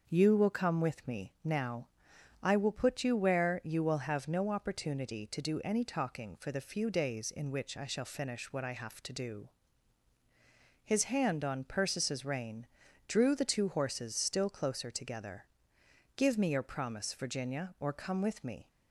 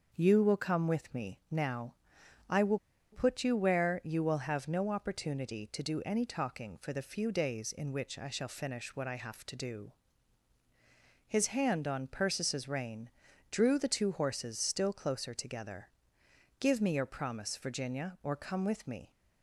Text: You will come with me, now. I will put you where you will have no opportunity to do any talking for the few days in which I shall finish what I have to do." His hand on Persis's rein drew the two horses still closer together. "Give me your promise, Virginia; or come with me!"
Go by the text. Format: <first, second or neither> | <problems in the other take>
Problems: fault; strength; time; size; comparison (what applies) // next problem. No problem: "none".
first | starts louder than the rest; until 1.1 s; 6 dB; also in the first // pauses between "will" and "put"; slight; at 2.7 s; 0.33 s long // pauses between "rein" and "drew"; at 13.1 s; 0.40 s long; also in the first